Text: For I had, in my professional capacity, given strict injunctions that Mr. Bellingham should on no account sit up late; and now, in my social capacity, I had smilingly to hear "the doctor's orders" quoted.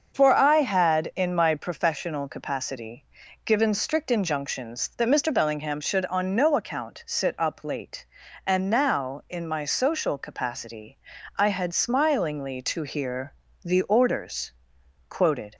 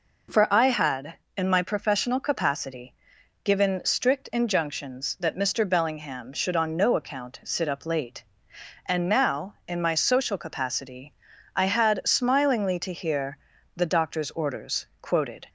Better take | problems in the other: second | starts louder than the rest; until 1.2 s; 6.5 dB // pauses between "hear" and "the"; slight; at 13.3 s; 0.32 s long; slight in the second // skips "doctor's"; at 13.8 s // pauses between "orders" and "quoted"; noticeable; at 14.5 s; 0.56 s long; slight in the second

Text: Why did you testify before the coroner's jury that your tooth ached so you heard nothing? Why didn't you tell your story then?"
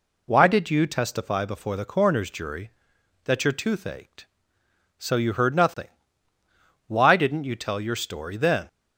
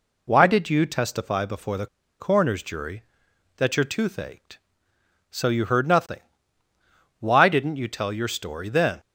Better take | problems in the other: first | pauses between "the" and "coroner's"; slight; at 1.8 s; 0.33 s long

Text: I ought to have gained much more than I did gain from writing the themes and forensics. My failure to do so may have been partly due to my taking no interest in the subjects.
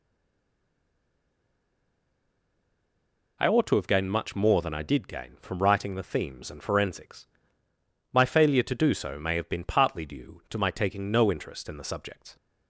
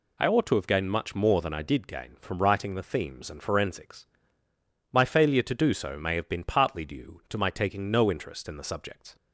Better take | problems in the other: second | stays silent before the first word; strong; until 3.3 s; 3.3 s long

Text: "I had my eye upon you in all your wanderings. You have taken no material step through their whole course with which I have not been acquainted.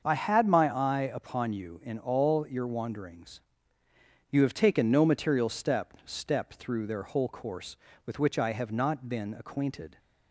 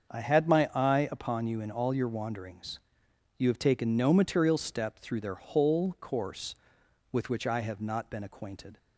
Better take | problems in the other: second | starts louder than the rest; until 1.0 s; 6.5 dB; also in the second // says "step" twice; at 6.0 s

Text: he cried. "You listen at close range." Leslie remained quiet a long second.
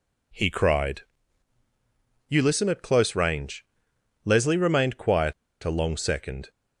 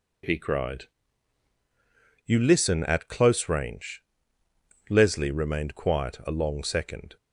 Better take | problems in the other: second | pauses between "quiet" and "a"; slight; at 5.3 s; 0.30 s long

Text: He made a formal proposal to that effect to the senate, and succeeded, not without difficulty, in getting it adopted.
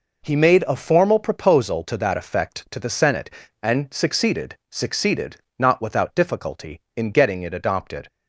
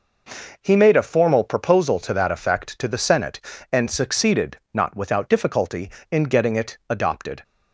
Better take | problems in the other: second | says "succeeded" twice; at 4.6 s

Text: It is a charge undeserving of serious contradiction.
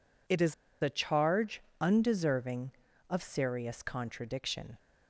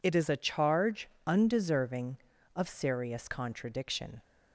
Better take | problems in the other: second | pauses between "is" and "a"; slight; at 0.5 s; 0.29 s long // pauses between "charge" and "undeserving"; slight; at 1.6 s; 0.20 s long; slight in the second

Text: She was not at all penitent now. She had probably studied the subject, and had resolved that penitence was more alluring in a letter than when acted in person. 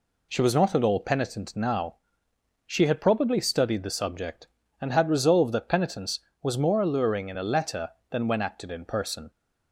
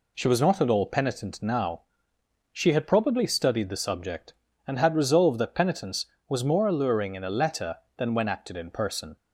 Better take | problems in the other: neither | none

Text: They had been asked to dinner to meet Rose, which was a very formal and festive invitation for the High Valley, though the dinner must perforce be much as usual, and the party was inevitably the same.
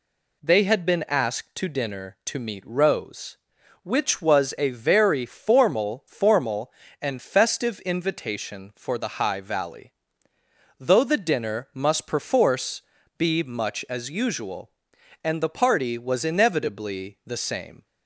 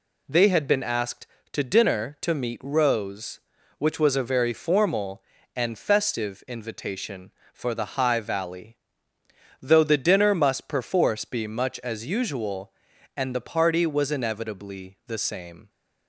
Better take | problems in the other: second | says "formal" twice; at 6.0 s // pauses between "perforce" and "be"; slight; at 12.8 s; 0.36 s long

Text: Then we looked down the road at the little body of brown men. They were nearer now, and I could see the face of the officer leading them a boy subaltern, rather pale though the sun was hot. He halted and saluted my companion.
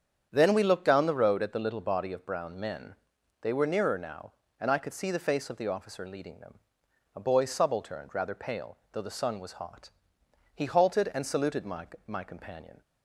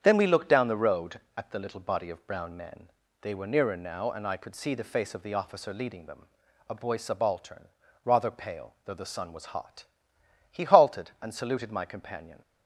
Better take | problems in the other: second | starts louder than the rest; strong; until 1.3 s; 8 dB; strong in the second // pauses between "them" and "a"; noticeable; at 6.5 s; 0.60 s long; noticeable in the second // says "my" twice; at 12.0 s

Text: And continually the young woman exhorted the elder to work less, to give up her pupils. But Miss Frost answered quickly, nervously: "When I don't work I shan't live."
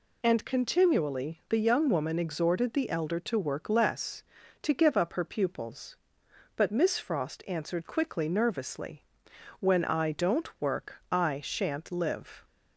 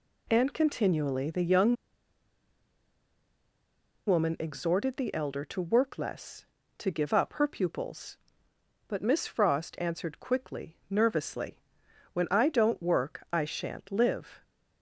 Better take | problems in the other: first | pauses between "young" and "woman"; strong; at 1.7 s; 2.3 s long

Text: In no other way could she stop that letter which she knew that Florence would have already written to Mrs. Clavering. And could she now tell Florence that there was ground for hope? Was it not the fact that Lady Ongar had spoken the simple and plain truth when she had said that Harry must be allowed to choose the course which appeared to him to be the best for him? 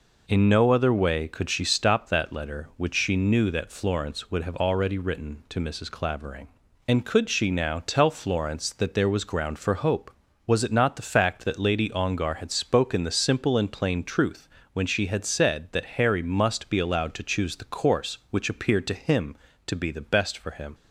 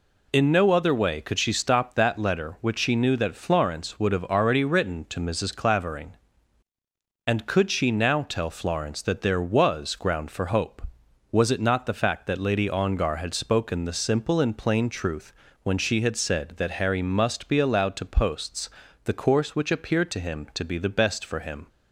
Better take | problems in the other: first | pauses between "truth" and "when"; slight; at 15.3 s; 0.30 s long; slight in the first // says "posts" for "choose"; at 18.0 s

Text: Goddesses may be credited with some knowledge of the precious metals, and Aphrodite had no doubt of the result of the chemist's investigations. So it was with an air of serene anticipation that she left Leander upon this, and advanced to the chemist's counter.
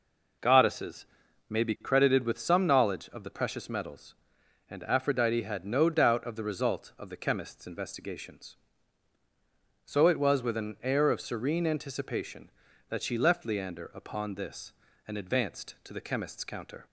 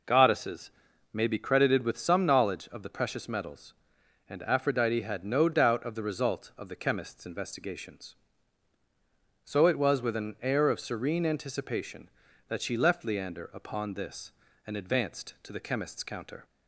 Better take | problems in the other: neither | pauses between "Goddesses" and "may"; the same in both

